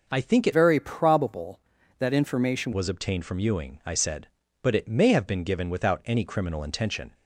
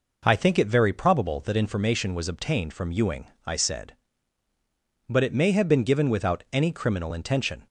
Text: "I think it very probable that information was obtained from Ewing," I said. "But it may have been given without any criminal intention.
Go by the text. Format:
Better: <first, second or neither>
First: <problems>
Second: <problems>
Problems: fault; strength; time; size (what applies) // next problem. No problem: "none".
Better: second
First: changes voice from "very" to "information"; from 0.5 to 2.7 s; 2.2 s long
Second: none